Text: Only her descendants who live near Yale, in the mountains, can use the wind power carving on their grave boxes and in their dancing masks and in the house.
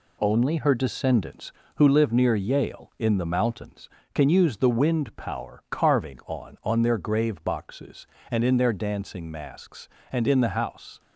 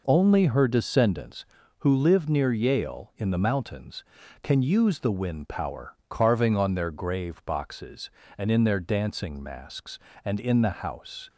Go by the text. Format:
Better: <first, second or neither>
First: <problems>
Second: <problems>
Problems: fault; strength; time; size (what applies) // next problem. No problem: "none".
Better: second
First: says "on" twice; at 6.6 s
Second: none